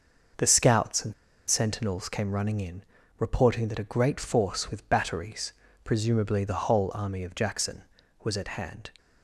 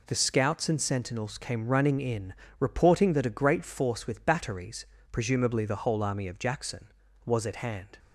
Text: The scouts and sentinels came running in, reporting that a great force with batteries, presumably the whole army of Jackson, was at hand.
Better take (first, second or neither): second